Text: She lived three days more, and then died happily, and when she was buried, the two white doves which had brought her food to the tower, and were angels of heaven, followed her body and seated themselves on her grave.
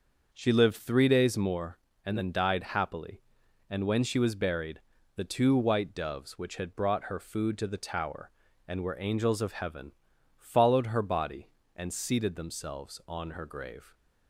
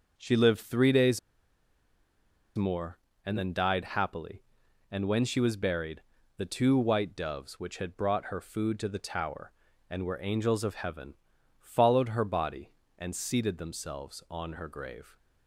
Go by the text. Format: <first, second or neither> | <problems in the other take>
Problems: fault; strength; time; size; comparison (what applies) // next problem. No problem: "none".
first | starts louder than the rest; noticeable; until 1.1 s; 6 dB; noticeable in the first // pauses between "days" and "more"; strong; at 1.1 s; 1.3 s long